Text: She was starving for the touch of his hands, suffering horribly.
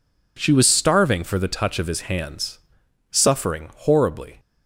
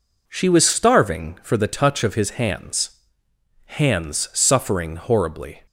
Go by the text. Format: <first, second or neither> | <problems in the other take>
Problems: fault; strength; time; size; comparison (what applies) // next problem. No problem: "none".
first | says "hands" twice; at 3.6 s